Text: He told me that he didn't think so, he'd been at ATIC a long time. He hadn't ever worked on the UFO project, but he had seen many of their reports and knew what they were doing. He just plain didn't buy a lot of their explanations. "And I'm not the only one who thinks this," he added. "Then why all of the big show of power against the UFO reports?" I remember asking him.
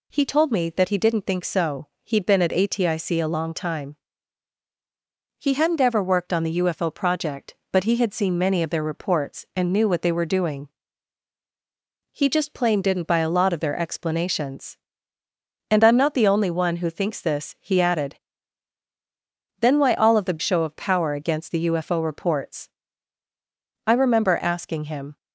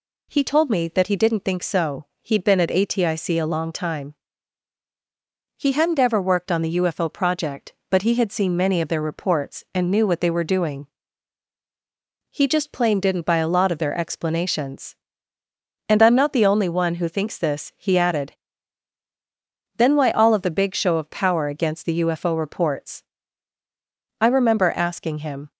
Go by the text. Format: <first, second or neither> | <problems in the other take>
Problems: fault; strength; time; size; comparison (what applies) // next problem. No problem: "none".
second | skips "big"; at 20.4 s